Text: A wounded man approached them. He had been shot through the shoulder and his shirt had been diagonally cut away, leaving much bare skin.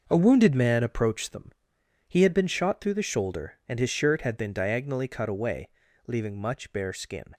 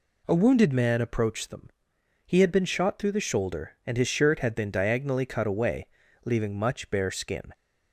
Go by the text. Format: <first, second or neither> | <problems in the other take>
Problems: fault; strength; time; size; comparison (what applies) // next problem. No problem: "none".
second | gets quieter; strong; throughout; 10.5 dB